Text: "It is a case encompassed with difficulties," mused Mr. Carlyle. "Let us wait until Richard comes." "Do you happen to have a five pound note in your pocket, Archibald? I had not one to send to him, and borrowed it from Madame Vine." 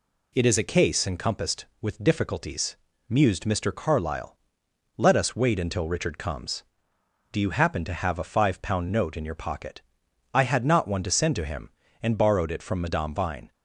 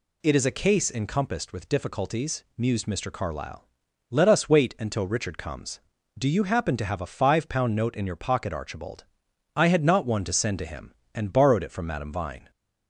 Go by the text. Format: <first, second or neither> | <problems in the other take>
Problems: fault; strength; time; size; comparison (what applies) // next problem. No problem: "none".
second | skips "Archibald"; at 10.0 s